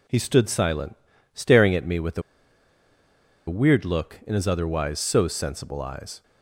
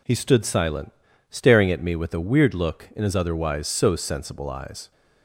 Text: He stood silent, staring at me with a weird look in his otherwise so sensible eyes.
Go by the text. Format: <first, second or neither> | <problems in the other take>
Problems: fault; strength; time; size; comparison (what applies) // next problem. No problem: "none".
second | pauses between "a" and "weird"; strong; at 2.2 s; 1.2 s long